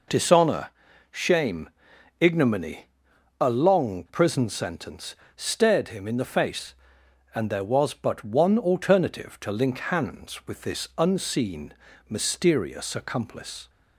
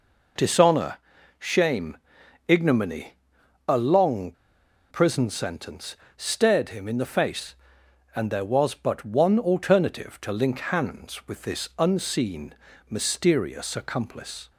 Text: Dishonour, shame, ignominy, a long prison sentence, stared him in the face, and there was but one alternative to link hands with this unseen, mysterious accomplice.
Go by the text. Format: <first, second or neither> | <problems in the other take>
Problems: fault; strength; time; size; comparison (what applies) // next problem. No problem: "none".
first | pauses between "long" and "prison"; noticeable; at 4.3 s; 0.57 s long